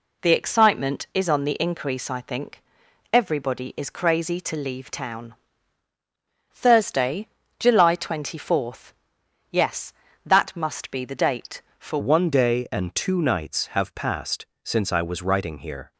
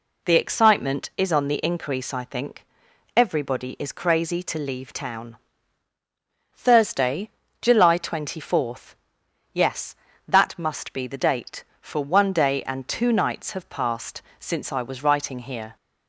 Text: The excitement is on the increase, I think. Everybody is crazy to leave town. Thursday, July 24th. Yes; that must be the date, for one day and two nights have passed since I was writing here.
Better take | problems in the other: second | changes voice at "one"; from 11.9 s on; 4.0 s long // pauses between "passed" and "since"; slight; at 14.4 s; 0.18 s long; slight in the second

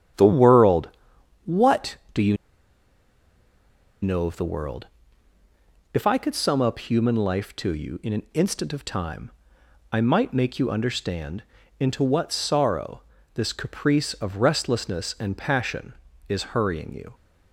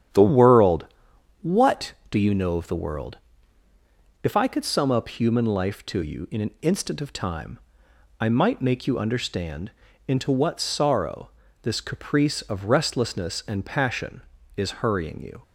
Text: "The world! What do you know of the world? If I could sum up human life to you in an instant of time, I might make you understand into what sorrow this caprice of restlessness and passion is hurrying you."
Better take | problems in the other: second | starts louder than the rest; strong; until 1.6 s; 9 dB; strong in the second // pauses between "you" and "know"; strong; at 2.3 s; 1.6 s long // pauses between "understand" and "into"; at 11.4 s; 0.38 s long; also in the second // pauses between "sorrow" and "this"; slight; at 13.0 s; 0.32 s long; slight in the second

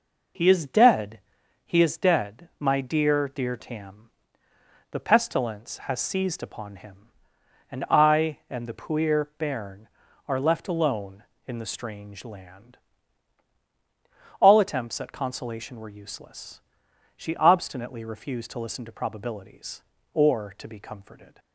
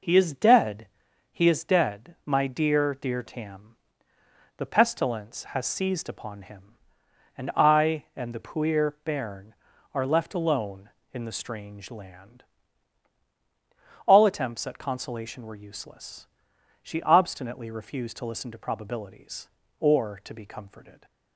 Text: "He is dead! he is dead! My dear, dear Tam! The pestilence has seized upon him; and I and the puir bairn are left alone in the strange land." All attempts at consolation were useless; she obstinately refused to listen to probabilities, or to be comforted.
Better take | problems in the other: neither | none

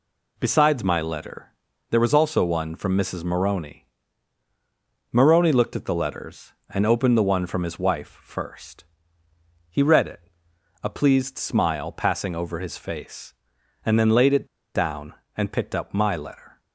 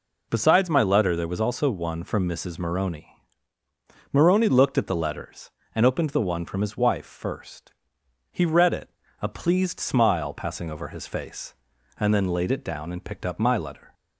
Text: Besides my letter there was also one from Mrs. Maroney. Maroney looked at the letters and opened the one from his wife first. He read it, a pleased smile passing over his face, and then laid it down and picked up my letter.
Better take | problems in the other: second | pauses between "letter" and "there"; at 1.5 s; 0.38 s long // pauses between "it" and "down"; slight; at 14.4 s; 0.27 s long

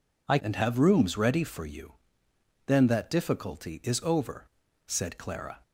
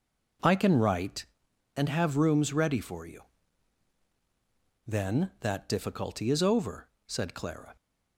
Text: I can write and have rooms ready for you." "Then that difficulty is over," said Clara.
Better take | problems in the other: second | skips "can write"; at 0.3 s

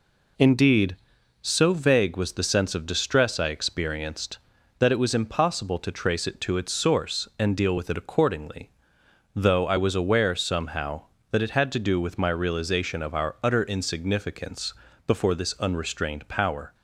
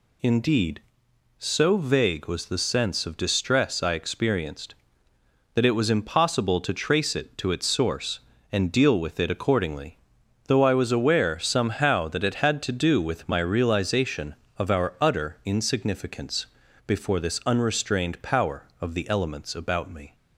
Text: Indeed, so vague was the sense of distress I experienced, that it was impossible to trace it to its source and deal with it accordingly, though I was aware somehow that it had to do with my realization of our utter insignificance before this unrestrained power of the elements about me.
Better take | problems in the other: second | pauses between "insignificance" and "before"; slight; at 14.7 s; 0.30 s long; also in the second // stops before "of the elements about me"; at 16.7 s

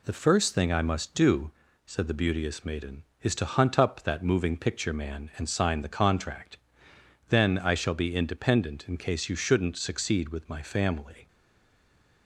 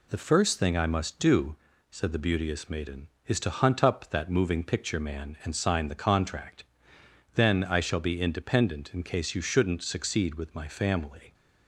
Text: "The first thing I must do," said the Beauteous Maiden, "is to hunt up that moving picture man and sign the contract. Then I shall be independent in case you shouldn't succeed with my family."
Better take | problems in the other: second | stays silent after the last word; from 11.2 s on; 1.0 s long

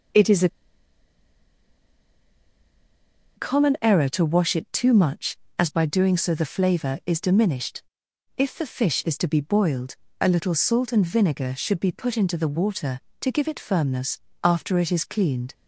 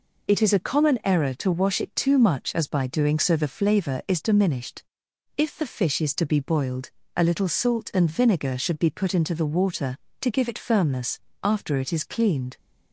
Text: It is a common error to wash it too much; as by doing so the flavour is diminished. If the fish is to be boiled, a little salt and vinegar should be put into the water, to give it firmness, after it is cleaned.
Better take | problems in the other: second | pauses between "a" and "common"; strong; at 0.4 s; 2.8 s long

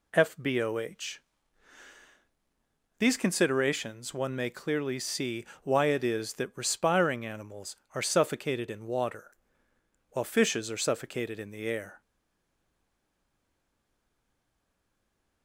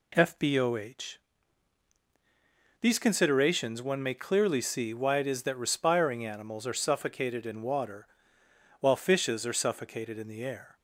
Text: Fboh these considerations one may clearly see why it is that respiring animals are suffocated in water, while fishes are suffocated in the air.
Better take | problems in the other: second | pauses between "Fboh" and "these"; strong; at 1.1 s; 1.8 s long; strong in the second // pauses between "see" and "why"; slight; at 5.4 s; 0.16 s long // stays silent after the last word; strong; from 12.0 s on; 3.4 s long

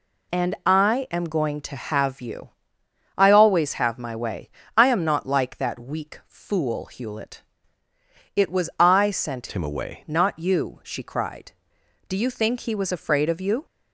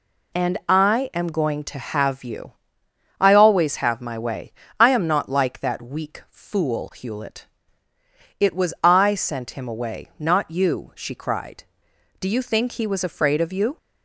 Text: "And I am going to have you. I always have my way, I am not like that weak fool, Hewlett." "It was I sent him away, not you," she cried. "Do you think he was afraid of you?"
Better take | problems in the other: second | changes voice from "him" to "away"; from 9.5 to 9.9 s; 0.4 s long

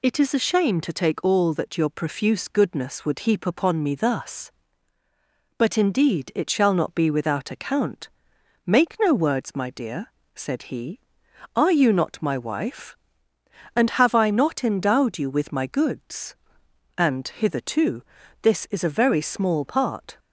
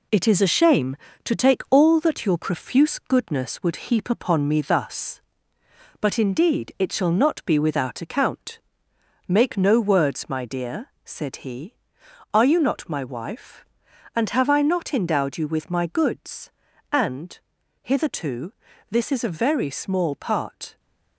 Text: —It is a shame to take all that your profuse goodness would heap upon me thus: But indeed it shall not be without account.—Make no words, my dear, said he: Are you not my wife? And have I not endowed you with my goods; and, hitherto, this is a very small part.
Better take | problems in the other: first | gets quieter; noticeable; throughout; 5 dB

